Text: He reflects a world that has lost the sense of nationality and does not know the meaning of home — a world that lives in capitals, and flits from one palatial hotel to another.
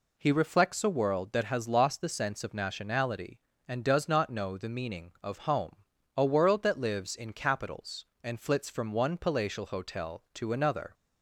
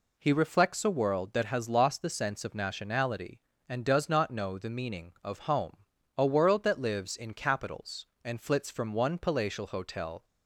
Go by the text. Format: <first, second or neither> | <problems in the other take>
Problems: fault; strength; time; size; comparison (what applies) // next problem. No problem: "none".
first | stops before "to another"; at 10.2 s